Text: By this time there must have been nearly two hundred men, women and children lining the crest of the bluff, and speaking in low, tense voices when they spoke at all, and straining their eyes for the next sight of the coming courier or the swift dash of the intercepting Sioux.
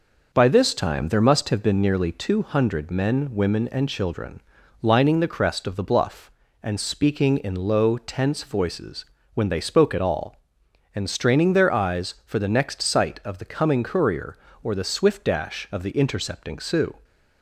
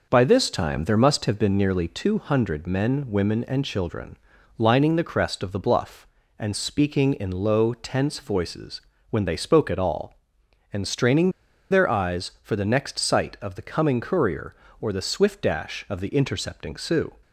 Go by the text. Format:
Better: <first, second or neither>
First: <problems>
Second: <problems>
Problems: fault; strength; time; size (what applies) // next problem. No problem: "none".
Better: first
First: pauses between "children" and "lining"; at 4.4 s; 0.40 s long // pauses between "voices" and "when"; slight; at 9.0 s; 0.30 s long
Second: pauses between "children" and "lining"; at 4.1 s; 0.40 s long // pauses between "voices" and "when"; slight; at 8.8 s; 0.30 s long // pauses between "straining" and "their"; at 11.2 s; 0.41 s long